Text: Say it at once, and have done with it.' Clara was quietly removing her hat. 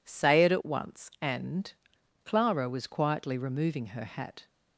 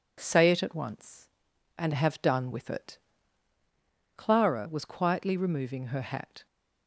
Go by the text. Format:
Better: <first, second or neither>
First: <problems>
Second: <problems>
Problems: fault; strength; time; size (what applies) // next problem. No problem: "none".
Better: second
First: skips "have done with it"; at 1.9 s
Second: none